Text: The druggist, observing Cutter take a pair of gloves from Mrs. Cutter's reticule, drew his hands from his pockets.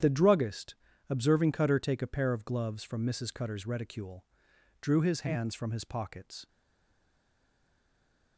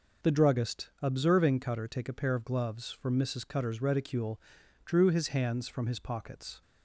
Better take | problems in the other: second | starts louder than the rest; strong; until 1.3 s; 9.5 dB // stays silent after the last word; noticeable; from 6.4 s on; 1.9 s long

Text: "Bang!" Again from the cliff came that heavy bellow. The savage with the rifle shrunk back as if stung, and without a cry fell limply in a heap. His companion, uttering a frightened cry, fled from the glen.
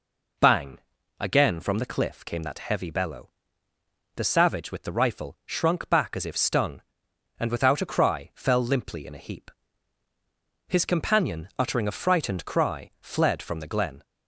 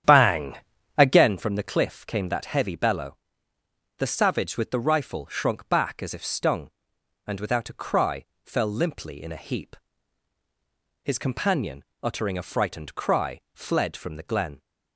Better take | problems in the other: first | starts louder than the rest; strong; until 1.4 s; 10 dB // pauses between "cry" and "fell"; slight; at 8.2 s; 0.18 s long

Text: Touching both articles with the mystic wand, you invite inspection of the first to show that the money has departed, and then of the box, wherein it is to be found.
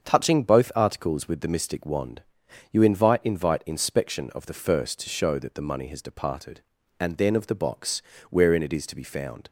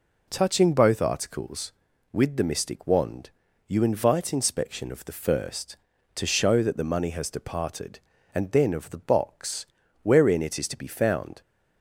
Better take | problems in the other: second | starts louder than the rest; strong; until 1.0 s; 7 dB // says "invite" twice; at 3.2 s

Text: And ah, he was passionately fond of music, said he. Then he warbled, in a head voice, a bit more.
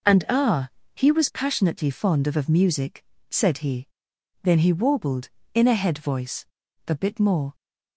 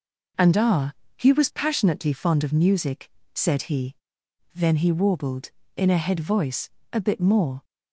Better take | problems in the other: second | says "of" twice; at 2.3 s

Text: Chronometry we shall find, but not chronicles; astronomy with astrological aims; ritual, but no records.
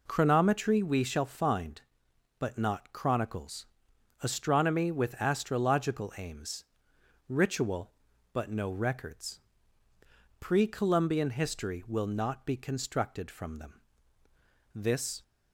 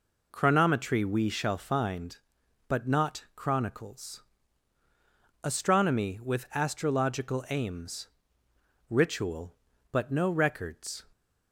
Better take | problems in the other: second | goes on to say "Pre Columbian history will not be constructed from them This"; strong; from 10.4 s on; 4.8 s long

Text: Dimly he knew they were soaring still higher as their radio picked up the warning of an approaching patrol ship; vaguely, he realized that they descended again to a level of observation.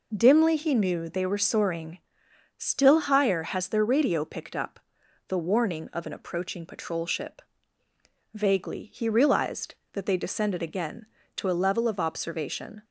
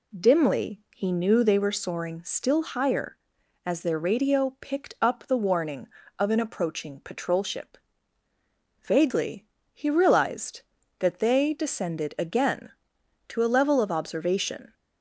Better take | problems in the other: second | pauses between "soaring" and "still"; noticeable; at 1.9 s; 0.58 s long // says "has" for "as"; at 3.4 s // pauses between "up" and "the"; noticeable; at 4.7 s; 0.52 s long

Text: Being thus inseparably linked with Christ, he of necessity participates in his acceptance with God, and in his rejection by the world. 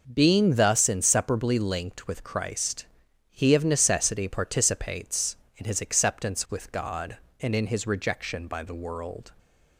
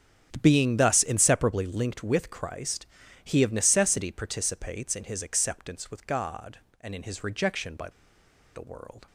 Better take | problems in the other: first | starts louder than the rest; strong; until 1.4 s; 9 dB; noticeable in the first // pauses between "by" and "the"; noticeable; at 7.8 s; 0.66 s long

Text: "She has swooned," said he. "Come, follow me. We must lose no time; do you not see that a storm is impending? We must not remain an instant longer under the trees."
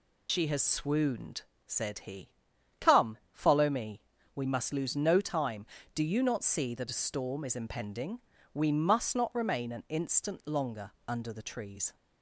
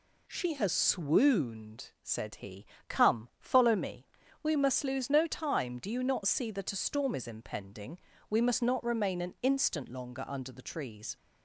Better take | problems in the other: second | loses the start of "She"; at 0.2 s; 95 ms // pauses between "longer" and "under"; slight; at 10.9 s; 0.18 s long

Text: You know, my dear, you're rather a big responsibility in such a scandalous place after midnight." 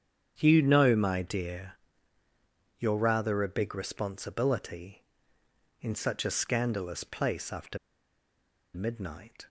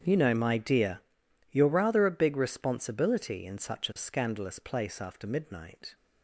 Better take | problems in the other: second | starts louder than the rest; strong; until 1.3 s; 8 dB; strong in the second // pauses between "after" and "midnight"; noticeable; at 7.7 s; 0.97 s long

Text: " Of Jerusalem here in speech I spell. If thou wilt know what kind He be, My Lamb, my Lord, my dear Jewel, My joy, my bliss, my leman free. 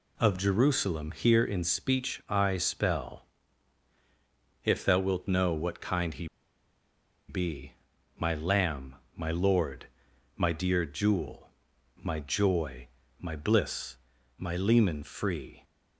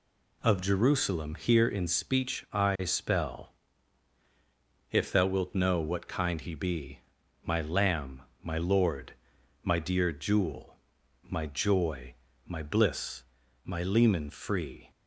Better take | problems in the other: second | pauses between "He" and "be"; at 6.2 s; 1.0 s long

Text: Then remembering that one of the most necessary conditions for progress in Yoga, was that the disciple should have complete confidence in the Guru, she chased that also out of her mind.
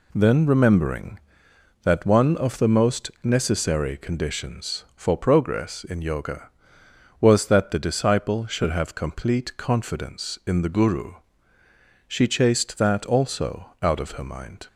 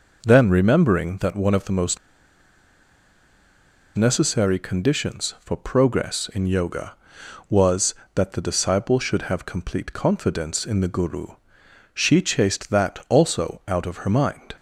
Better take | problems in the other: first | pauses between "most" and "necessary"; strong; at 1.9 s; 1.9 s long

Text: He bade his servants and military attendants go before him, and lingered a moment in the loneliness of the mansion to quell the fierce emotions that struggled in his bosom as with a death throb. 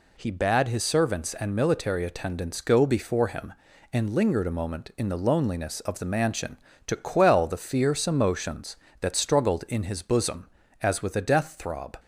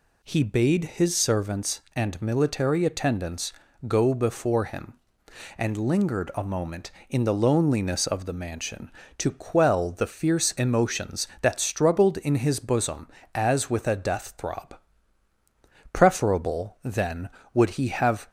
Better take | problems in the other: first | pauses between "attendants" and "go"; slight; at 3.5 s; 0.36 s long // goes on to say "Preferable then would he have"; strong; from 15.9 s on; 2.3 s long

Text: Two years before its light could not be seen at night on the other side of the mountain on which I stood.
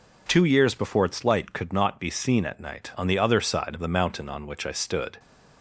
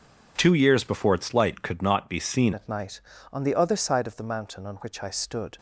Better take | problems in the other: first | changes voice at "at"; from 2.5 s on; 3.0 s long

